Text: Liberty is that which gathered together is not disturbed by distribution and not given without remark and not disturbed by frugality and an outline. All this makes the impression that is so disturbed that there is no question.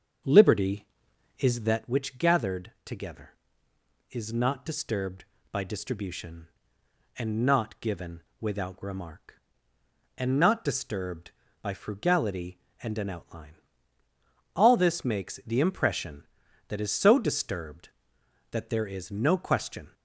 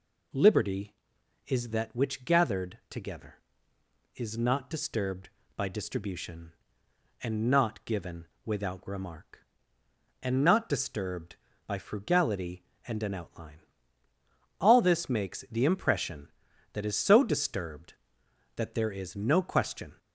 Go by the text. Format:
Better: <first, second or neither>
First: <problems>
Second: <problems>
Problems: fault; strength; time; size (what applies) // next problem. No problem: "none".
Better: second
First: starts louder than the rest; until 1.9 s; 7 dB // pauses between "gathered" and "together"; slight; at 2.6 s; 0.16 s long // pauses between "given" and "without"; slight; at 8.2 s; 0.18 s long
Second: pauses between "given" and "without"; slight; at 8.2 s; 0.18 s long